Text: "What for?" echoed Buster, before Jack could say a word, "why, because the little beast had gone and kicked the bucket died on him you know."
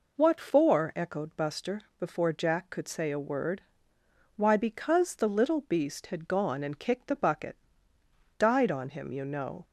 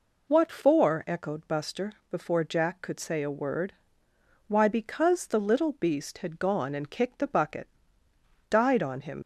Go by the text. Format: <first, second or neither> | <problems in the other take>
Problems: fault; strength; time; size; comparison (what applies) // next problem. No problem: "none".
first | pauses between "bucket" and "died"; noticeable; at 7.6 s; 0.82 s long; noticeable in the first // stops before "you know"; at 9.2 s